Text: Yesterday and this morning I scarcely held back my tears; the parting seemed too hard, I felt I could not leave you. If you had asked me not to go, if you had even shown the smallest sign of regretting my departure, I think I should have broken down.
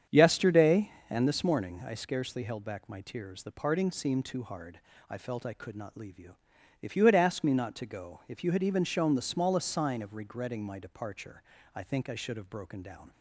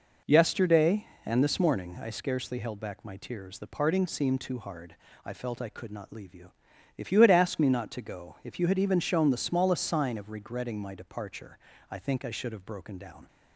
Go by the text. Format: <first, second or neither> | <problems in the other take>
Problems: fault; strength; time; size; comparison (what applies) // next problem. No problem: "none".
second | starts louder than the rest; strong; until 1.3 s; 8 dB